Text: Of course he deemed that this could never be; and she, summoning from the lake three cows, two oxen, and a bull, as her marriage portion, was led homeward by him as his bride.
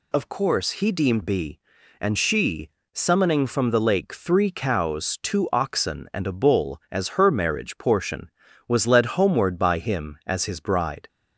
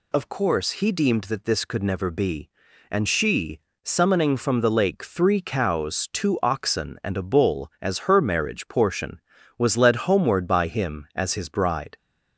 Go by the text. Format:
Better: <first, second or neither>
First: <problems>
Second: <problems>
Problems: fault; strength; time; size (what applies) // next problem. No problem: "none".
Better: second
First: skips "that this could never"; at 1.2 s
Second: none